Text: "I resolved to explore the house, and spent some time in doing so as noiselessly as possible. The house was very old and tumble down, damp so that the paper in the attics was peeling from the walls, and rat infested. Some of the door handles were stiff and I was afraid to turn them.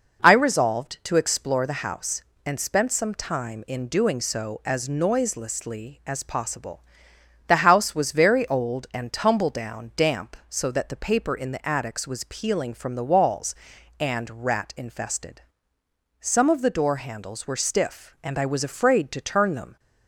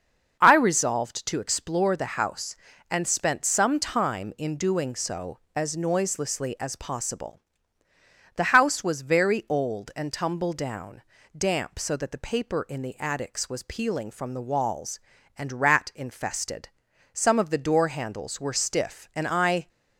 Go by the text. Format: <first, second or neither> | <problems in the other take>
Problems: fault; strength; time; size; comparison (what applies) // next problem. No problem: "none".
first | starts louder than the rest; until 1.4 s; 6.5 dB // stops before "was afraid to turn them"; at 19.6 s